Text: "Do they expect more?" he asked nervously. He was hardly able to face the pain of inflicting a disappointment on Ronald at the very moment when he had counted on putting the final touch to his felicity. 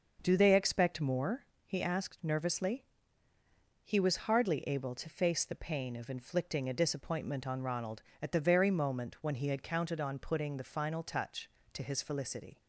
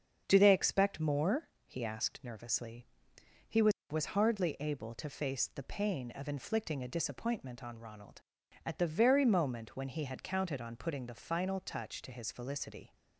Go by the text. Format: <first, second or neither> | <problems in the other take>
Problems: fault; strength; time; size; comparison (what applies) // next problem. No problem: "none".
first | starts louder than the rest; until 1.2 s; 7 dB; noticeable in the first // says "was" twice; at 3.9 s